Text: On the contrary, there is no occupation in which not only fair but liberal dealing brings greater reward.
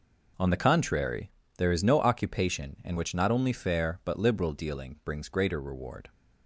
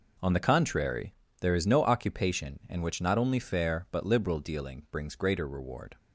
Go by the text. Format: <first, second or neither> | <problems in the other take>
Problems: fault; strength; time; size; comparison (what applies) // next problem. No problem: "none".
neither | none